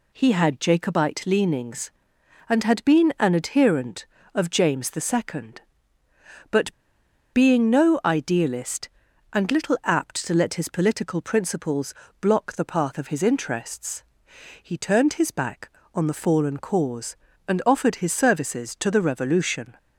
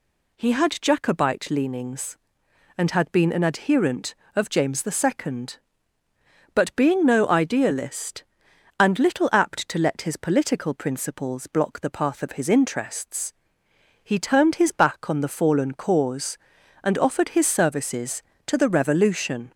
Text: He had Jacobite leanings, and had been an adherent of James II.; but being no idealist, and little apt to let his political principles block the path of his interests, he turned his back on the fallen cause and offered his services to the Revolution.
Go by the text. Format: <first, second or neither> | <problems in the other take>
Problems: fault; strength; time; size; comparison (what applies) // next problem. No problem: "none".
second | pauses between "but" and "being"; noticeable; at 6.7 s; 0.63 s long // pauses between "principles" and "block"; slight; at 11.9 s; 0.30 s long